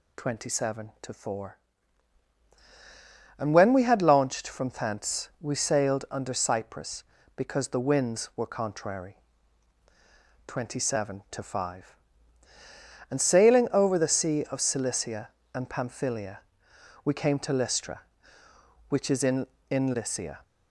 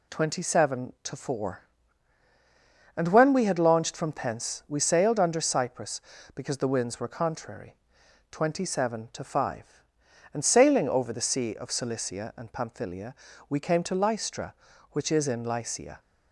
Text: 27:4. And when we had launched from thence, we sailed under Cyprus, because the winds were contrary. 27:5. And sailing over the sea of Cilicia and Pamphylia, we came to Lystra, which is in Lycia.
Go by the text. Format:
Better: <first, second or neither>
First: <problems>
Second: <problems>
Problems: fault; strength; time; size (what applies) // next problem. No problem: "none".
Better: second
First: says "in" twice; at 19.7 s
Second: none